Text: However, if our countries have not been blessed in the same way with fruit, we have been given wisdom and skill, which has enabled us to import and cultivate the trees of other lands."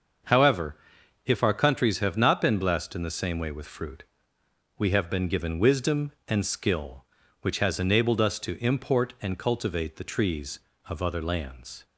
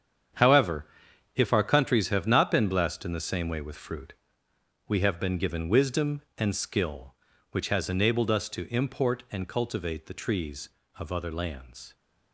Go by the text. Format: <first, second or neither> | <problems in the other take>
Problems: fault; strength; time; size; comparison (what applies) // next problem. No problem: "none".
first | gets quieter; strong; throughout; 10.5 dB // starts louder than the rest; strong; until 1.8 s; 8 dB; also in the first